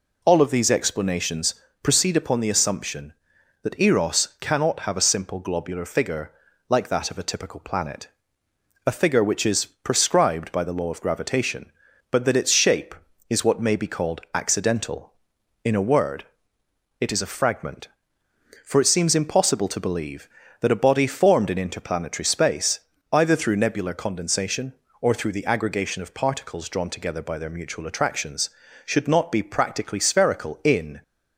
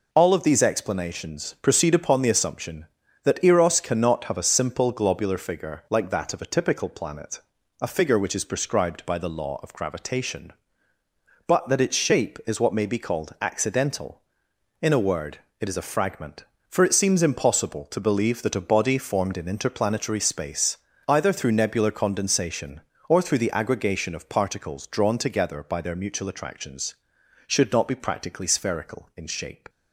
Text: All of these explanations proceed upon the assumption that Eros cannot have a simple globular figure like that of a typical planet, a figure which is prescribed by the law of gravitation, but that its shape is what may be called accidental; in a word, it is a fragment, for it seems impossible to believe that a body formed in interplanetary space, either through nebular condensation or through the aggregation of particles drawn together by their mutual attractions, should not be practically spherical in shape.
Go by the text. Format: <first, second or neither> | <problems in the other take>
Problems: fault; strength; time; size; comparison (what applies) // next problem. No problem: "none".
second | pauses between "explanations" and "proceed"; slight; at 1.5 s; 0.28 s long // pauses between "figure" and "like"; at 6.3 s; 0.38 s long // stops before "shape"; at 31.0 s